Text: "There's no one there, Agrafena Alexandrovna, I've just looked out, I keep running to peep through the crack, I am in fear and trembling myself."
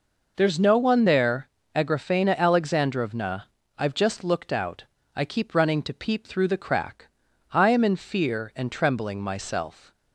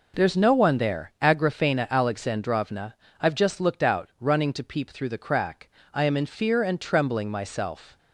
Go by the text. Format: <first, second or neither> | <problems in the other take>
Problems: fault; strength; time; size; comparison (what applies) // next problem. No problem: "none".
first | skips "I keep"; at 4.1 s